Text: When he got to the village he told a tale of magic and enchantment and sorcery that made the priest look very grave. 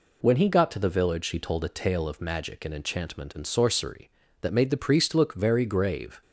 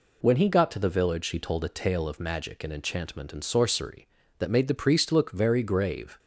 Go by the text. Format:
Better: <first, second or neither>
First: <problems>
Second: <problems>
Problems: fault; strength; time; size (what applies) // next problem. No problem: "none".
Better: neither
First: none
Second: none